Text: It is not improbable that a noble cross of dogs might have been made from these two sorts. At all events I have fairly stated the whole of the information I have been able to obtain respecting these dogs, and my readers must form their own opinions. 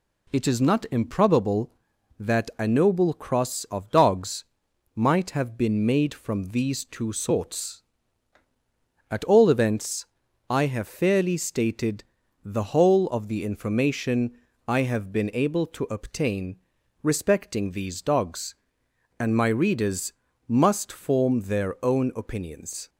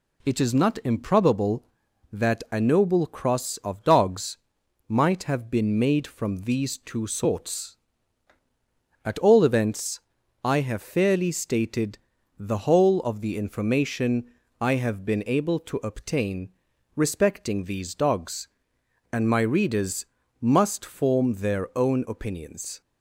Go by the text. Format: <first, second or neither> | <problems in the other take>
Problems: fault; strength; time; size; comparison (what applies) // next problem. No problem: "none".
neither | pauses between "dogs" and "might"; noticeable; the same in both // pauses between "events" and "I"; the same in both // pauses between "stated" and "the"; the same in both // pauses between "information" and "I"; slight; the same in both // pauses between "obtain" and "respecting"; noticeable; the same in both // pauses between "readers" and "must"; the same in both